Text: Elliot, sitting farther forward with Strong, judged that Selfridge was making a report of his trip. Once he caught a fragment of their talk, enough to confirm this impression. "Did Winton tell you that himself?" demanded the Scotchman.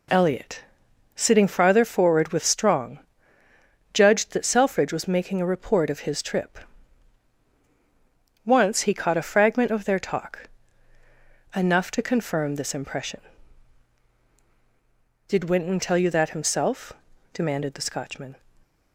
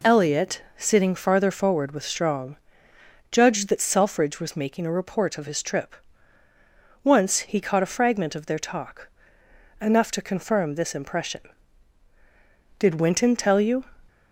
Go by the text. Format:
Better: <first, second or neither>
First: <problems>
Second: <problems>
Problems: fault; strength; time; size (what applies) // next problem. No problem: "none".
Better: first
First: none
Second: stops before "that himself demanded the Scotchman"; at 14.0 s